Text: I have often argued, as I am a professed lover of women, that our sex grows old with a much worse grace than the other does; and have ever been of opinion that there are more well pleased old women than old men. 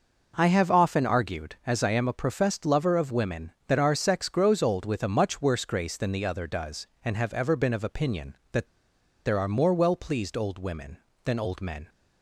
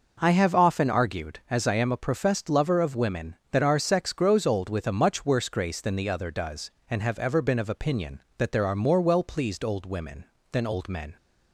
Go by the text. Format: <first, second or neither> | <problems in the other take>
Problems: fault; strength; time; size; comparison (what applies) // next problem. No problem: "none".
second | pauses between "that" and "there"; noticeable; at 8.6 s; 0.58 s long